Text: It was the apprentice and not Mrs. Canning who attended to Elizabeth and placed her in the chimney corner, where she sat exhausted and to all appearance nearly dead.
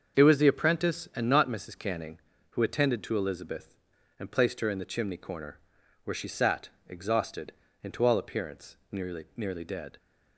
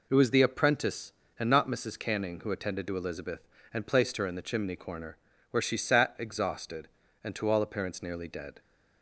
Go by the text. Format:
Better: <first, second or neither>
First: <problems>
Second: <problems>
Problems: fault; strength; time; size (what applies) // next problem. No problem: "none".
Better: second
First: starts louder than the rest; until 1.2 s; 6.5 dB // pauses between "sat" and "exhausted"; slight; at 6.6 s; 0.18 s long // pauses between "appearance" and "nearly"; slight; at 8.7 s; 0.16 s long // says "nearly" twice; at 9.3 s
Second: none